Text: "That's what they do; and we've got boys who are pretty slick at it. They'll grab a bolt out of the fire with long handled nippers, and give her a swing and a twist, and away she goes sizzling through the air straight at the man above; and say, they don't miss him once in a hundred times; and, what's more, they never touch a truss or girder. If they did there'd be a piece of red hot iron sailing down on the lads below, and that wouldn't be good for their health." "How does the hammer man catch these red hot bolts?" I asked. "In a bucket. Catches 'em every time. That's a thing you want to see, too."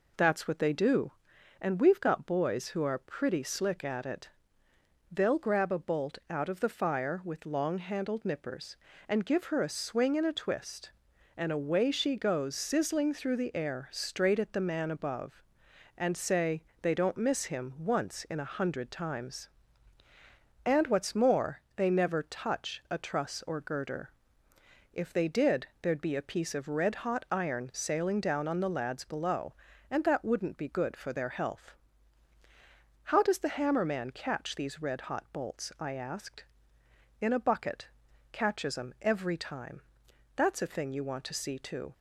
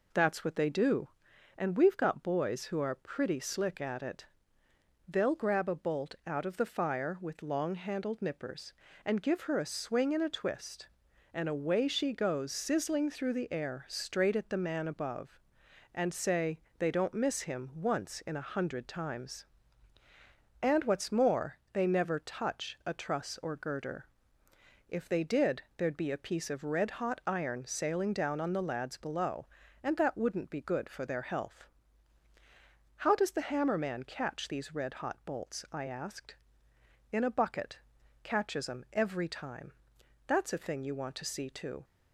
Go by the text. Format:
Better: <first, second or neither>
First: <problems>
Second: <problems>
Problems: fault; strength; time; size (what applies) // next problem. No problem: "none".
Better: neither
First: pauses between "did" and "there'd"; slight; at 25.6 s; 0.16 s long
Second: pauses between "did" and "there'd"; slight; at 25.6 s; 0.16 s long